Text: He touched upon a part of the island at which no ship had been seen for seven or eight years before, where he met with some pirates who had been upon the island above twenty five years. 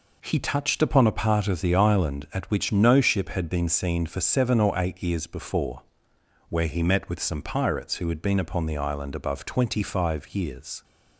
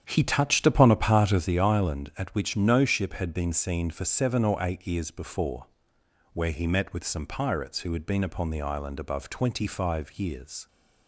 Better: first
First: none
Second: starts louder than the rest; strong; until 1.5 s; 9 dB

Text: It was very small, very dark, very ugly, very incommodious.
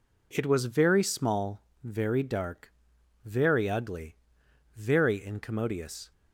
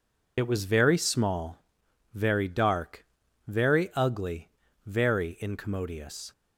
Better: first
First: none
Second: loses the start of "It"; at 0.3 s; 60 ms

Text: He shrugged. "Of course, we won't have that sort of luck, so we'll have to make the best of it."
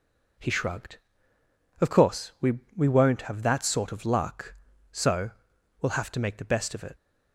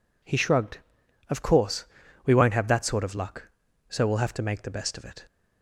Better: second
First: says "we" twice; at 2.7 s // pauses between "so" and "we'll"; noticeable; at 5.3 s; 0.50 s long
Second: none

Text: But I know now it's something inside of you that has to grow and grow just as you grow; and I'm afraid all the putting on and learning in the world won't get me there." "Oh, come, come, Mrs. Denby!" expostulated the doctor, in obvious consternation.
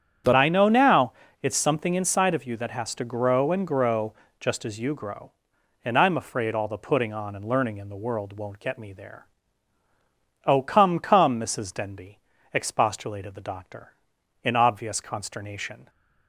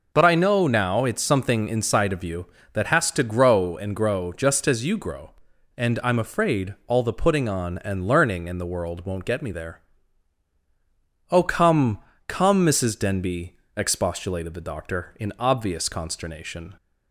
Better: second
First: starts louder than the rest; strong; until 1.5 s; 8 dB // changes voice at "I"; from 0.3 s on; 15.5 s long // pauses between "now" and "it's"; slight; at 1.1 s; 0.28 s long // pauses between "grow" and "just"; slight; at 4.1 s; 0.26 s long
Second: none

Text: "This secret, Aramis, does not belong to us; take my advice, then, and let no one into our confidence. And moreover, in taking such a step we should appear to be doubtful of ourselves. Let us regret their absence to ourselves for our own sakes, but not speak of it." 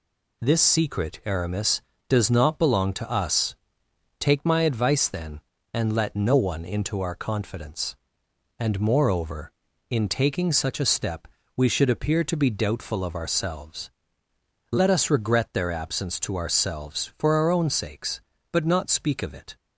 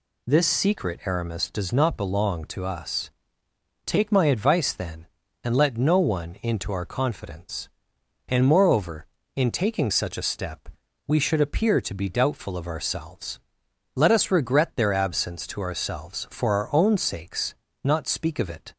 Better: first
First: pauses between "step" and "we"; slight; at 11.2 s; 0.28 s long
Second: pauses between "step" and "we"; at 10.6 s; 0.38 s long // skips "but"; at 17.6 s

